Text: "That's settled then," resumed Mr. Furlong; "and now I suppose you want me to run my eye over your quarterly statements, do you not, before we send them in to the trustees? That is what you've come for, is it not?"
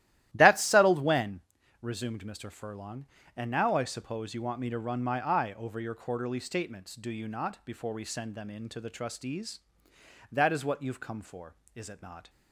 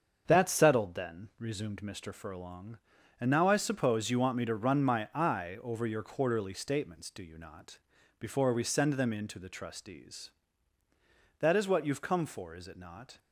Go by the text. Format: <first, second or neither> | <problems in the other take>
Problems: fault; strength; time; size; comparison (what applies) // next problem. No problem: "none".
second | starts louder than the rest; strong; until 1.3 s; 14 dB; also in the second // says "when" for "then"; at 1.0 s